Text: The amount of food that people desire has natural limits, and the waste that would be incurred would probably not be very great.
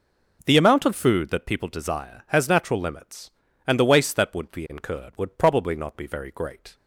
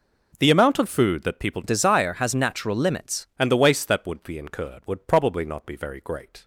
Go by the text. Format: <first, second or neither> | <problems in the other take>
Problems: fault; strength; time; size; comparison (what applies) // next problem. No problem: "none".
first | changes voice from "desire" to "limits"; from 1.6 to 3.2 s; 1.6 s long